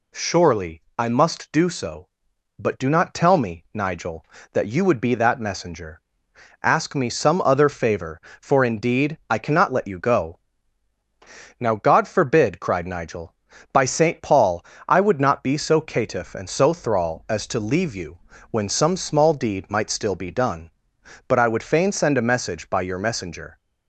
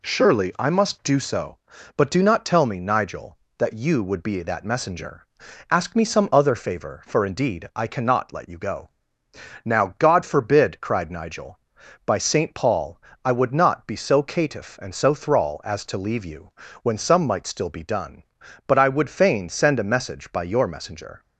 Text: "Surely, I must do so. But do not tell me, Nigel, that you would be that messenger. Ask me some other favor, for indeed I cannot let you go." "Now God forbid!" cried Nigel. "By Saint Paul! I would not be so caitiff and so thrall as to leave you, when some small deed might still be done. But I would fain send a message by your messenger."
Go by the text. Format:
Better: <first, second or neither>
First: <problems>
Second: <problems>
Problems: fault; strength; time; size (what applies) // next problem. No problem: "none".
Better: first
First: none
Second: skips "small deed"; at 17.2 s